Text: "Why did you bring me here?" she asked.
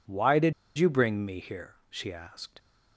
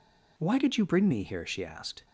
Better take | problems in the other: second | pauses between "did" and "you"; slight; at 0.5 s; 0.25 s long

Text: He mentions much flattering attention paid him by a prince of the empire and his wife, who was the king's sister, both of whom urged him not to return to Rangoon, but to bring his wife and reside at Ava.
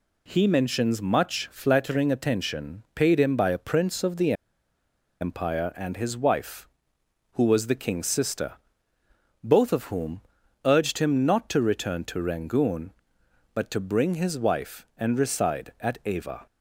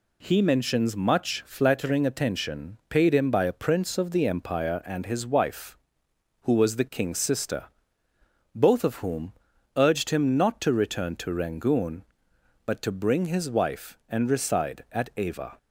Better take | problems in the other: second | pauses between "the" and "empire"; noticeable; at 4.3 s; 0.88 s long // pauses between "whom" and "urged"; at 10.2 s; 0.42 s long; also in the second

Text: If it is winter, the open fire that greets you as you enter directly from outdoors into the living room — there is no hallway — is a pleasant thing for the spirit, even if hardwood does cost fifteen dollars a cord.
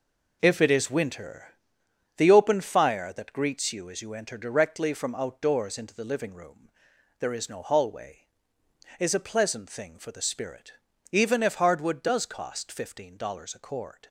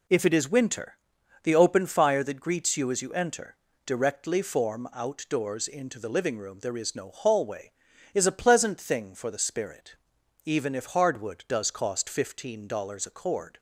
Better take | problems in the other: first | pauses between "enter" and "directly"; slight; at 3.5 s; 0.28 s long // says "form" for "from"; at 4.4 s

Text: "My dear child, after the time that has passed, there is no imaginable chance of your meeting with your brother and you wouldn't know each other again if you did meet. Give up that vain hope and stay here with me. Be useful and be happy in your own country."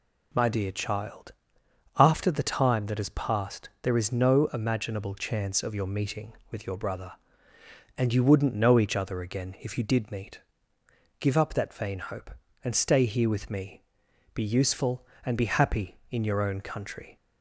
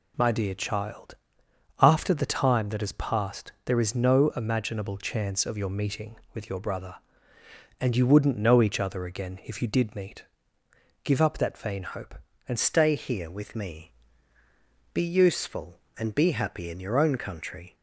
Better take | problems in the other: first | changes voice at "stay"; from 12.5 s on; 5.2 s long

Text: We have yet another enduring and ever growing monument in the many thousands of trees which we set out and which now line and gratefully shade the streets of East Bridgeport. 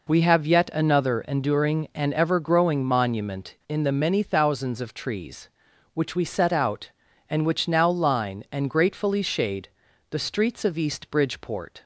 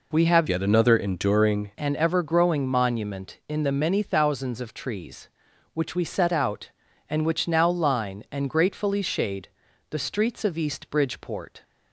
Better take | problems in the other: first | changes voice from "yet" to "enduring"; from 0.4 to 1.7 s; 1.3 s long // pauses between "shade" and "the"; at 9.4 s; 0.40 s long; also in the first

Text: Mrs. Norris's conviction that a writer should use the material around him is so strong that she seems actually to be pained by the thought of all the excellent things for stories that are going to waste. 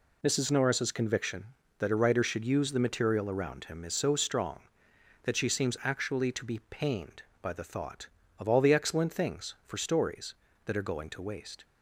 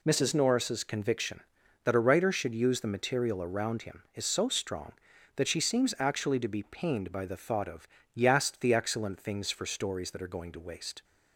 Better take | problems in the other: first | says "yast" for "all"; at 8.1 s

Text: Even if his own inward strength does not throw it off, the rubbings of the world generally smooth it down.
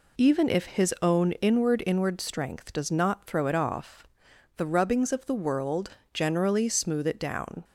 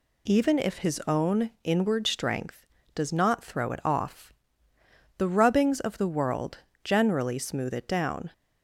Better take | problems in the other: second | says "inward" twice; at 1.8 s // pauses between "world" and "generally"; slight; at 5.8 s; 0.22 s long; slight in the second

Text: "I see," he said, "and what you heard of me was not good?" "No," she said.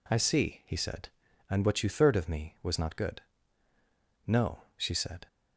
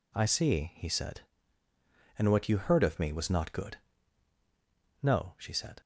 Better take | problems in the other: second | says "third" for "heard"; at 1.8 s

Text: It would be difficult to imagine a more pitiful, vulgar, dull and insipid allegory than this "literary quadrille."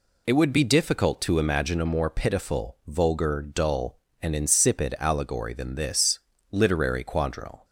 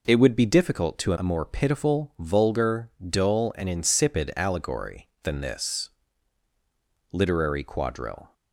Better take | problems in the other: first | skips "imagine"; at 1.1 s // pauses between "this" and "literary"; at 5.8 s; 1.2 s long; slight in the first

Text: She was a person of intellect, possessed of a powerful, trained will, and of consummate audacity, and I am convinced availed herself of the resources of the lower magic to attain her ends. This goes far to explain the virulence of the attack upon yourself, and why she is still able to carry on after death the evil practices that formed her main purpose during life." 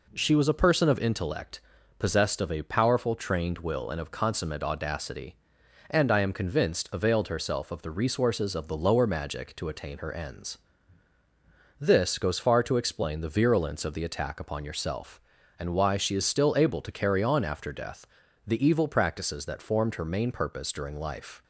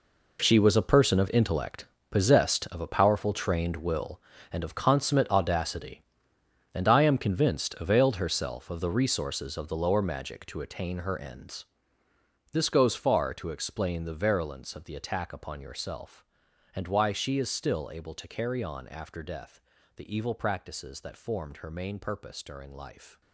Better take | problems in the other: first | gets quieter; strong; throughout; 13.5 dB // pauses between "death" and "the"; slight; at 19.6 s; 0.36 s long; also in the first

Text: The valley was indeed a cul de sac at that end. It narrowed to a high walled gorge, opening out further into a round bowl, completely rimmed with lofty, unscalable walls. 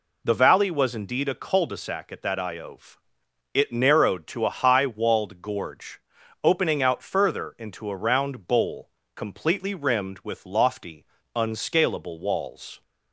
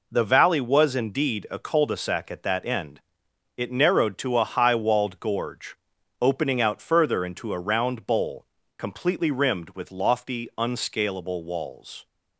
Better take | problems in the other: second | says "iove" for "end"; at 2.3 s

